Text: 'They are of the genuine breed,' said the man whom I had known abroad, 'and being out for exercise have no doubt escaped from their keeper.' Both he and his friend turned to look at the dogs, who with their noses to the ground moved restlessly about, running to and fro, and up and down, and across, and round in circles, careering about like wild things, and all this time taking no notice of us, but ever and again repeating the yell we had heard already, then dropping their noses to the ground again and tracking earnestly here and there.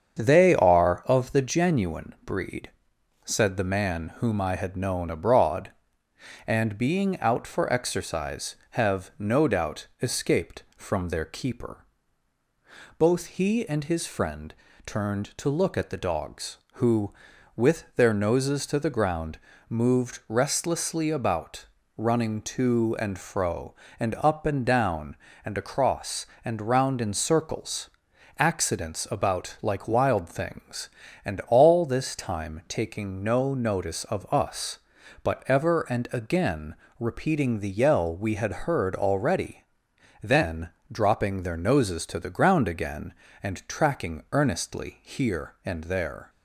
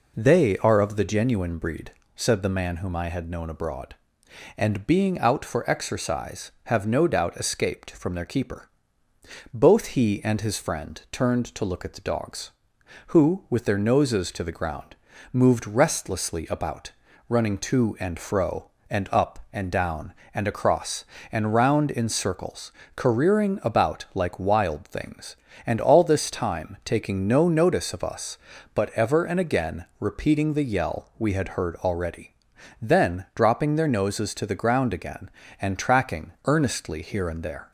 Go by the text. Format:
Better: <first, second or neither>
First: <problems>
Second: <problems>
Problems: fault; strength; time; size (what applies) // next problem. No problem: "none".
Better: second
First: starts louder than the rest; strong; until 1.2 s; 7.5 dB // pauses between "doubt" and "escaped"; slight; at 9.8 s; 0.16 s long // pauses between "friend" and "turned"; slight; at 14.5 s; 0.32 s long // pauses between "ground" and "moved"; slight; at 19.3 s; 0.32 s long // says "accidents" for "careering"; at 28.3 s // pauses between "again" and "repeating"; slight; at 36.7 s; 0.24 s long // pauses between "then" and "dropping"; slight; at 40.6 s; 0.22 s long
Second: pauses between "ground" and "moved"; at 14.9 s; 0.38 s long